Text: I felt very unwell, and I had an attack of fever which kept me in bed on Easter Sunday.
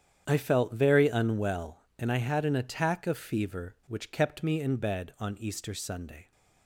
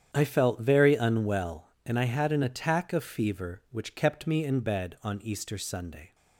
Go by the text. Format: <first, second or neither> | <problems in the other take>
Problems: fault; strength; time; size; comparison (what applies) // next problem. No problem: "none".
neither | starts louder than the rest; strong; the same in both